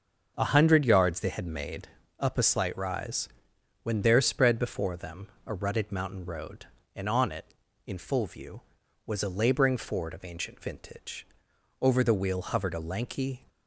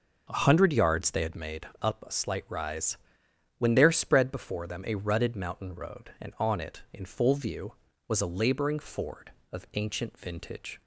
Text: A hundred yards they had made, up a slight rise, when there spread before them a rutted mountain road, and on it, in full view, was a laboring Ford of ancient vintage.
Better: second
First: starts louder than the rest; until 1.3 s; 6.5 dB // pauses between "them" and "a"; slight; at 5.2 s; 0.18 s long // goes on to say "Over the wheel hovered a lanky"; from 11.8 s on; 1.6 s long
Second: starts louder than the rest; noticeable; until 1.3 s; 6 dB

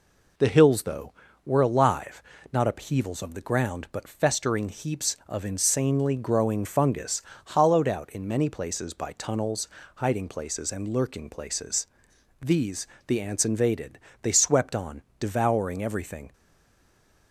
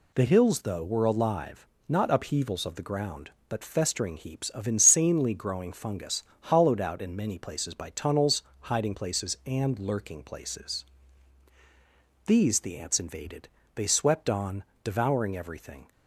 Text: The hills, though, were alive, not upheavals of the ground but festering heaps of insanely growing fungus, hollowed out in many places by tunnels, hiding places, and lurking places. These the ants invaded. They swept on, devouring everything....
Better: second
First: pauses between "These" and "the"; slight; at 12.8 s; 0.20 s long // stays silent after the last word; from 16.3 s on; 1.0 s long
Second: none

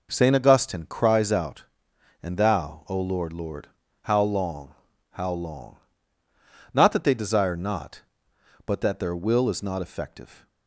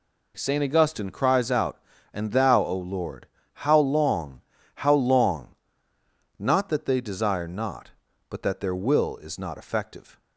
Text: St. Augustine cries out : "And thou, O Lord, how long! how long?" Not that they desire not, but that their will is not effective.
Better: second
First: says "Lord" twice; at 3.3 s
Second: none

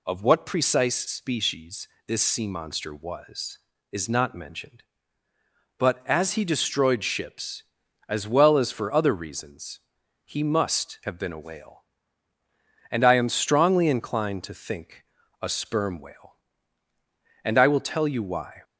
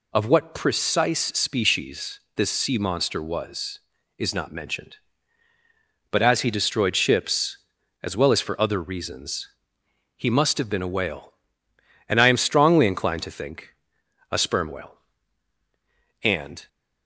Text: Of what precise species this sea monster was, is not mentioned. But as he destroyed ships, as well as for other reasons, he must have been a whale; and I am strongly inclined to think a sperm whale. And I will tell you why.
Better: first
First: pauses between "species" and "this"; slight; at 1.8 s; 0.20 s long // pauses between "think" and "a"; slight; at 15.0 s; 0.36 s long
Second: pauses between "species" and "this"; slight; at 2.1 s; 0.16 s long // pauses between "think" and "a"; noticeable; at 13.7 s; 0.58 s long // stops before "I will tell you why"; at 16.6 s

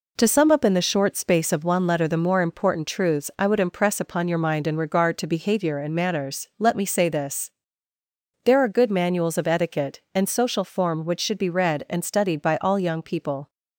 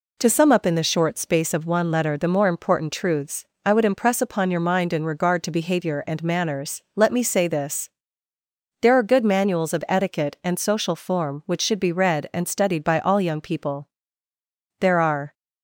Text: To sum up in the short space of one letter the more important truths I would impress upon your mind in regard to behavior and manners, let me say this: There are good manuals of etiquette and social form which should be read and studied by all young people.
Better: first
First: none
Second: pauses between "truths" and "I"; slight; at 3.4 s; 0.20 s long // goes on to say "There are"; from 14.7 s on; 0.54 s long

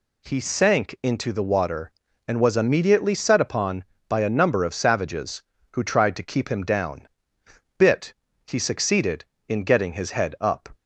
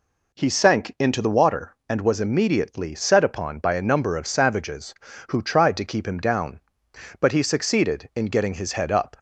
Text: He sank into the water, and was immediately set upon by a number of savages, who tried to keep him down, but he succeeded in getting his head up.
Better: second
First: says "bit" for "but"; at 7.7 s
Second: none

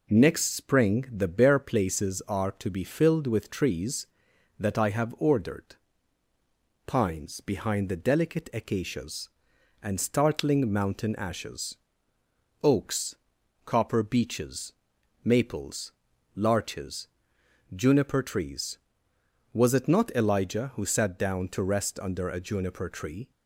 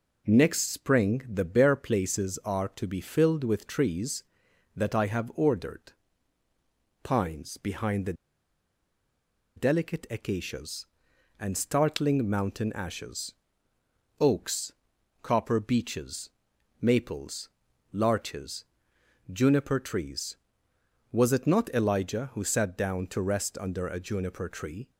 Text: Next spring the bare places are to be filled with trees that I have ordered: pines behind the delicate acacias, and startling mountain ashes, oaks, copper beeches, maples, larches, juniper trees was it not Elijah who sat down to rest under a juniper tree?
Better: first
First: none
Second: pauses between "the" and "delicate"; strong; at 8.1 s; 1.4 s long

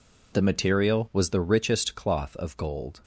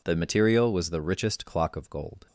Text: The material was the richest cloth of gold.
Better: first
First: none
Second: says "clock" for "cloth"; at 1.4 s

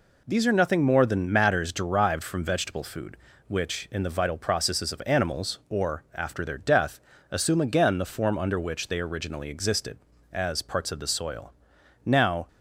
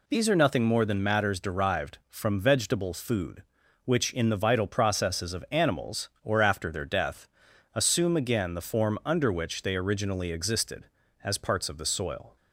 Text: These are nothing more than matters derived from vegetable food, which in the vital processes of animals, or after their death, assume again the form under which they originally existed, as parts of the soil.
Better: second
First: goes on to say "Now"; slight; from 12.0 s on; 0.42 s long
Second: none

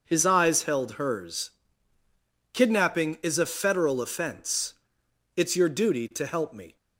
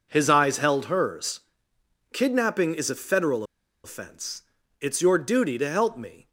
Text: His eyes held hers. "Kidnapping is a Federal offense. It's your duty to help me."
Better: first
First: none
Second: pauses between "Federal" and "offense"; at 3.4 s; 0.40 s long

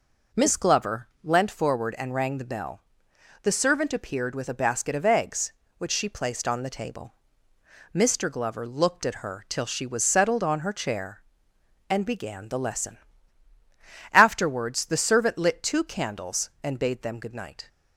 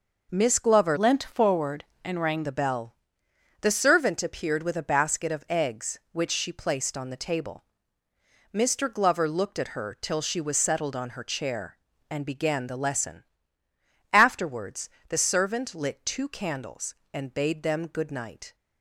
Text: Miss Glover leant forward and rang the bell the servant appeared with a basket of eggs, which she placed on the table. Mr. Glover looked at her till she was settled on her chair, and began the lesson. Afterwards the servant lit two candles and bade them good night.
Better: first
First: pauses between "bell" and "the"; noticeable; at 2.8 s; 0.62 s long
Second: changes voice from "leant" to "rang"; from 0.9 to 2.4 s; 1.5 s long // pauses between "bell" and "the"; noticeable; at 2.9 s; 0.66 s long // pauses between "Afterwards" and "the"; slight; at 14.8 s; 0.20 s long

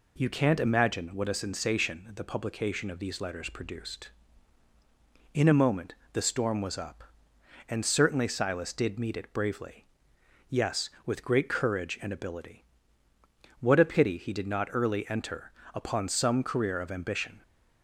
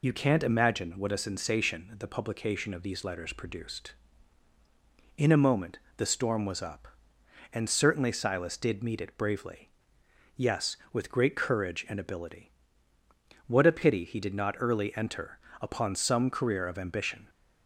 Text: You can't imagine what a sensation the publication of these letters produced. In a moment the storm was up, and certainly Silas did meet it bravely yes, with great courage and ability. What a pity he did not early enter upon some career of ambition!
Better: first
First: pauses between "moment" and "the"; slight; at 5.9 s; 0.20 s long // pauses between "bravely" and "yes"; noticeable; at 9.8 s; 0.66 s long // pauses between "enter" and "upon"; slight; at 15.5 s; 0.24 s long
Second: loses the start of "You"; at 0.0 s; 40 ms // pauses between "moment" and "the"; slight; at 5.7 s; 0.20 s long // pauses between "bravely" and "yes"; noticeable; at 9.6 s; 0.68 s long // pauses between "enter" and "upon"; slight; at 15.3 s; 0.24 s long

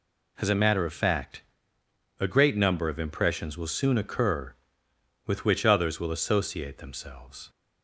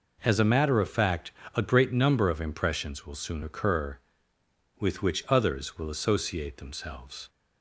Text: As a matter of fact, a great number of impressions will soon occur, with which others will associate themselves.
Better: neither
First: none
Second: none

